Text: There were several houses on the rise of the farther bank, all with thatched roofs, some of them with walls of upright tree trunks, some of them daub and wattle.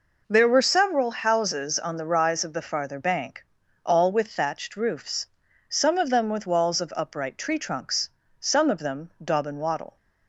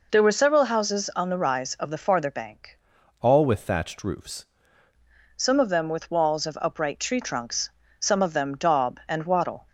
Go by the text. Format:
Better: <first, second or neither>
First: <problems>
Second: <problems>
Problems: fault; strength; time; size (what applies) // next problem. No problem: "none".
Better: first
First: none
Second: changes voice from "all" to "roofs"; from 3.1 to 4.4 s; 1.3 s long